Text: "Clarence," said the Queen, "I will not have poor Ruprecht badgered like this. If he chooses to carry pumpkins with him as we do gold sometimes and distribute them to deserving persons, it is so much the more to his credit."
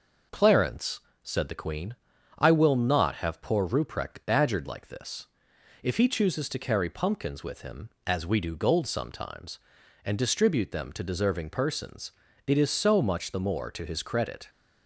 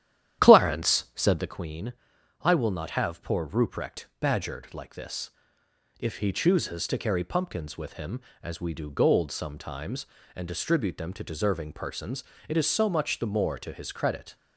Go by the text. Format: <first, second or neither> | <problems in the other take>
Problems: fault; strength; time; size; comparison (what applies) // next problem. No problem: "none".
first | starts louder than the rest; strong; until 1.6 s; 11 dB